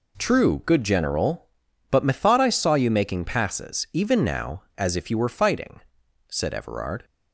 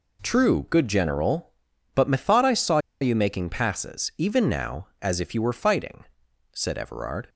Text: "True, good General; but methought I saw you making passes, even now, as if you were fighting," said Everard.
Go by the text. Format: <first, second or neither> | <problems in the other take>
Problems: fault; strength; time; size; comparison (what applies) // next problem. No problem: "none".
first | pauses between "saw" and "you"; slight; at 2.7 s; 0.22 s long